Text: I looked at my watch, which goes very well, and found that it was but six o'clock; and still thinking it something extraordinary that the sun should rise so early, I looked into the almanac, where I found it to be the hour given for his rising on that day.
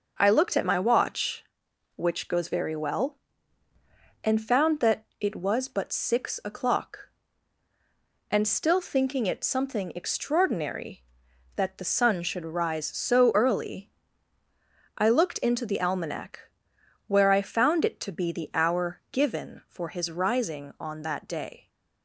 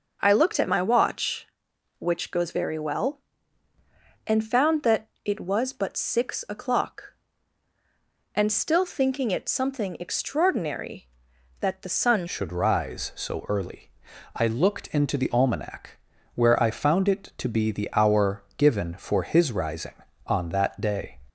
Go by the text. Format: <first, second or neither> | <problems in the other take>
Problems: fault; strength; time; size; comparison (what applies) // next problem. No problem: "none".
first | pauses between "that" and "it"; slight; at 5.0 s; 0.16 s long // changes voice at "should"; from 12.2 s on; 8.9 s long